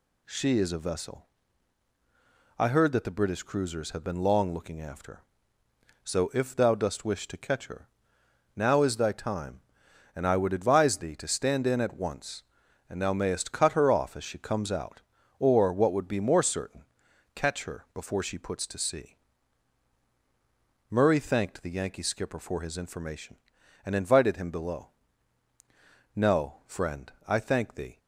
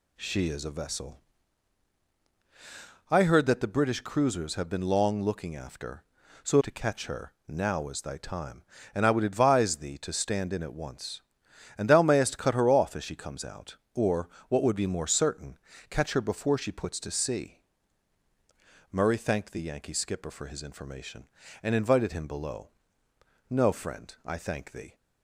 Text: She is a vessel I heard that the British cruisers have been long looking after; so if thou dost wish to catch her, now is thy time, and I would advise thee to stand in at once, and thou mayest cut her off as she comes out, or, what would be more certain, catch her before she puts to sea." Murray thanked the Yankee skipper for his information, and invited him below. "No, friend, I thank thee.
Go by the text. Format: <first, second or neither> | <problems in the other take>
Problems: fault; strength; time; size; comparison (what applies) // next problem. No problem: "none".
first | pauses between "vessel" and "I"; strong; at 1.2 s; 1.9 s long; strong in the first // skips "if thou dost wish"; at 6.5 s